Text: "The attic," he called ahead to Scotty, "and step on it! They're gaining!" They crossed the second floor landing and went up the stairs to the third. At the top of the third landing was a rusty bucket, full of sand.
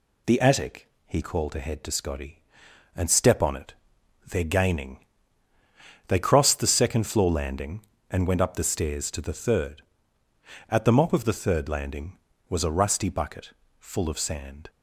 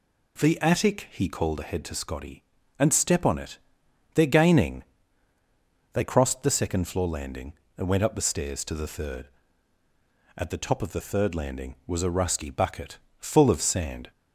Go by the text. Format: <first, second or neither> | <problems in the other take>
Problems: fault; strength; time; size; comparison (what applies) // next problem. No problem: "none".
second | says "mop" for "top"; at 10.9 s